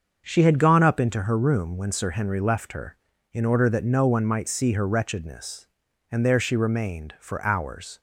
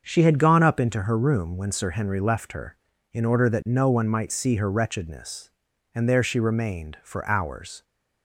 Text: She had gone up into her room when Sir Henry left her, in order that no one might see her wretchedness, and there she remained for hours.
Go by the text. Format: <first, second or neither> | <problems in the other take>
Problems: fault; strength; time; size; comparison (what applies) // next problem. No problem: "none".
neither | starts louder than the rest; the same in both